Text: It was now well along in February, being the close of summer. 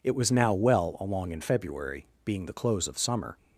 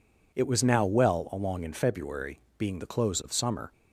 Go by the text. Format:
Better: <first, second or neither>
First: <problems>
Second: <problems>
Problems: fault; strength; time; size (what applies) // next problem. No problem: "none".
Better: neither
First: none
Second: none